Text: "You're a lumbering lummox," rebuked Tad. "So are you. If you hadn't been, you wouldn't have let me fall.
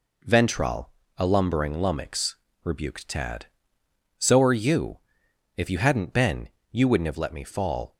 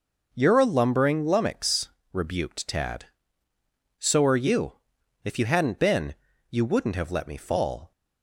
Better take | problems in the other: second | says "Ventral" for "You're"; at 0.2 s

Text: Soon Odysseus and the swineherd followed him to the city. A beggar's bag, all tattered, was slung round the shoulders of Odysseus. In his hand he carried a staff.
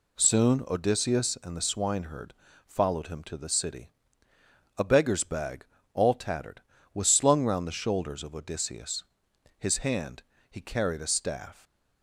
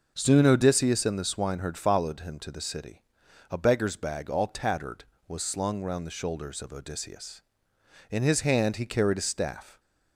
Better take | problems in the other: second | pauses between "swineherd" and "followed"; slight; at 2.3 s; 0.32 s long // skips "In"; at 9.3 s // pauses between "hand" and "he"; slight; at 10.2 s; 0.28 s long

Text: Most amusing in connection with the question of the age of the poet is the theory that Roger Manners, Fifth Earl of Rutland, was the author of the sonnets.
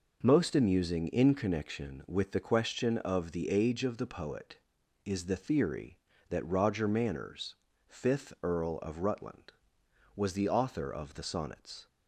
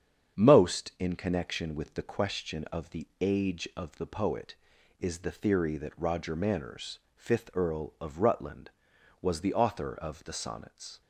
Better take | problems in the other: first | starts louder than the rest; strong; until 1.4 s; 8 dB // skips "amusing"; at 0.9 s

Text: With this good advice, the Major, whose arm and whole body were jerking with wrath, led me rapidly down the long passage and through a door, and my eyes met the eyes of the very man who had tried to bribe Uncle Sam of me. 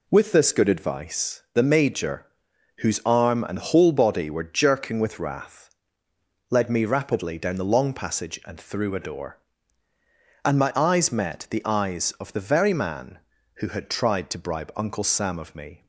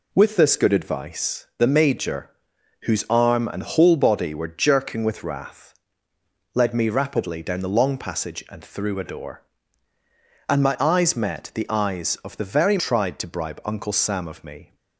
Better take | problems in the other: first | skips "man who had"; at 12.7 s

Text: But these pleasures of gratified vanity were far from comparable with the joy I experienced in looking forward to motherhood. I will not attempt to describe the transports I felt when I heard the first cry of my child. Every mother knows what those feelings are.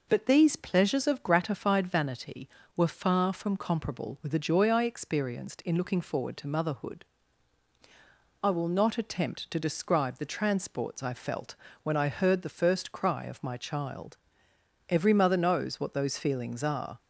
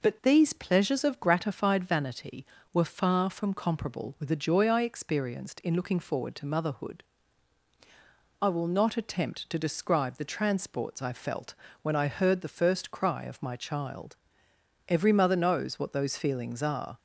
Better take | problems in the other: neither | pauses between "felt" and "when"; slight; the same in both

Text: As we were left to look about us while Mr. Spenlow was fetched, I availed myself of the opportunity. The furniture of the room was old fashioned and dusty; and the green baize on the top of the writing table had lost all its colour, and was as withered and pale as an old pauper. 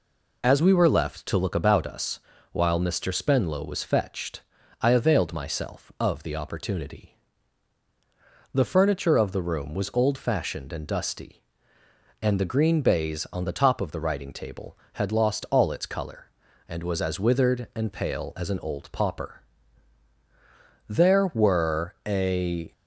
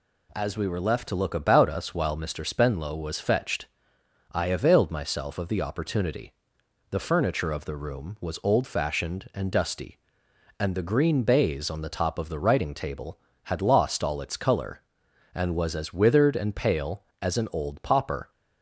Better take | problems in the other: second | pauses between "us" and "while"; slight; at 2.1 s; 0.32 s long // goes on to say "There were a"; strong; from 20.8 s on; 1.8 s long

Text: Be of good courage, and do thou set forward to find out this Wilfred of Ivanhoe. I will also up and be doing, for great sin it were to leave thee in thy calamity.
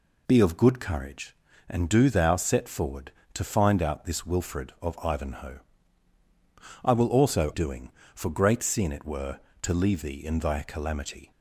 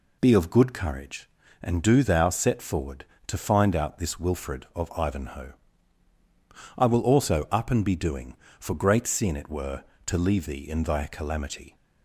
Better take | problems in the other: second | skips "up and be"; at 7.5 s

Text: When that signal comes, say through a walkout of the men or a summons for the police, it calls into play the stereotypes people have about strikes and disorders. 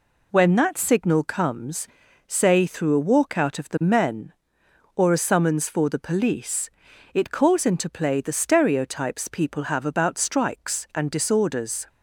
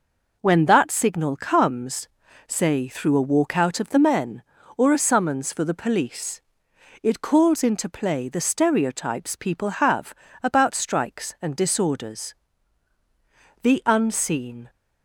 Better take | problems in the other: first | pauses between "have" and "about"; slight; at 10.1 s; 0.30 s long // goes on to say "The unseen"; noticeable; from 13.6 s on; 1.0 s long

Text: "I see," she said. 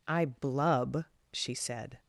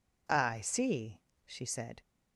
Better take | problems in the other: second | says "blub" for "see"; at 0.2 s

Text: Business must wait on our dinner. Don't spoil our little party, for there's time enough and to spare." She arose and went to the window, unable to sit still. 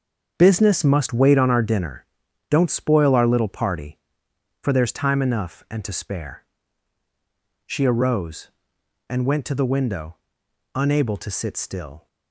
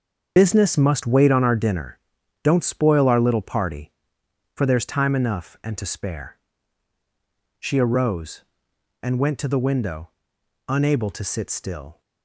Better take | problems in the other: first | loses the start of "Business"; at 0.3 s; 60 ms // starts louder than the rest; until 1.3 s; 7 dB; also in the first

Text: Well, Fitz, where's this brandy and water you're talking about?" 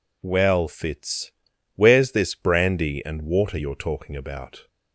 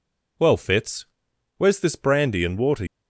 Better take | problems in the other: first | stops before "you're talking about"; at 2.8 s

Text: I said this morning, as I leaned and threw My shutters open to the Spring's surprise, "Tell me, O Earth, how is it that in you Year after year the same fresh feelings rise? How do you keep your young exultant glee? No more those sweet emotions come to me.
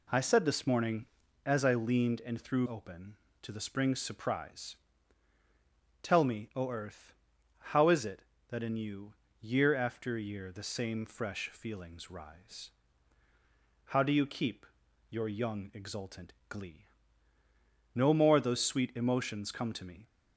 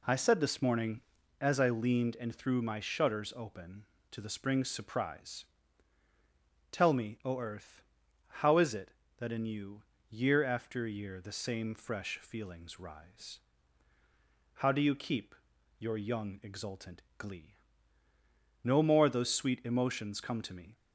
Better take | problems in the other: second | skips "My shutters"; at 2.6 s // pauses between "you" and "Year"; slight; at 9.1 s; 0.26 s long; slight in the second // pauses between "keep" and "your"; at 14.6 s; 0.42 s long; also in the second // pauses between "exultant" and "glee"; slight; at 16.3 s; 0.16 s long; slight in the second

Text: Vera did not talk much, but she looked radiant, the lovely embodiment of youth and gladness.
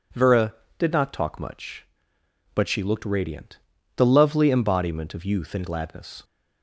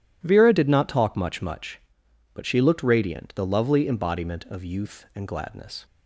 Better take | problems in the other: first | says "much" twice; at 1.4 s

